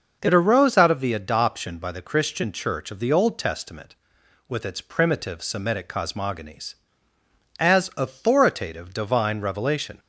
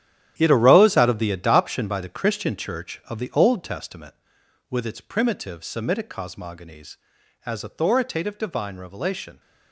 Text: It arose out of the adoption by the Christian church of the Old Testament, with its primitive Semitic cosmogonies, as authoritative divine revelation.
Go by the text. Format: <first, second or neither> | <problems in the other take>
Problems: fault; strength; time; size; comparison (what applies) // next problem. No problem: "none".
first | gets quieter; strong; throughout; 11.5 dB // starts louder than the rest; strong; until 1.3 s; 11 dB; noticeable in the first